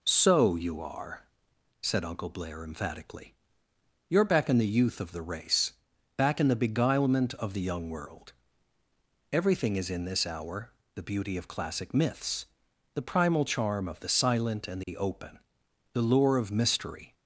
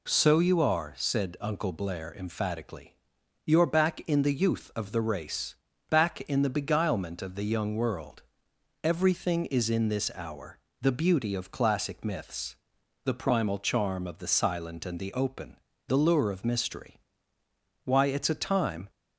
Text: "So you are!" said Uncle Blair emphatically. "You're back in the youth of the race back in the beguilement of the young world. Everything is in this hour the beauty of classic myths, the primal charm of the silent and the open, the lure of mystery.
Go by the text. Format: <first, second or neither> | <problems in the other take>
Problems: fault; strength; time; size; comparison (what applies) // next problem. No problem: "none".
first | pauses between "race" and "back"; slight; at 5.5 s; 0.32 s long; also in the first // pauses between "hour" and "the"; slight; at 10.5 s; 0.22 s long; slight in the first // goes on to say "Why it's a time"; noticeable; from 17.8 s on; 1.0 s long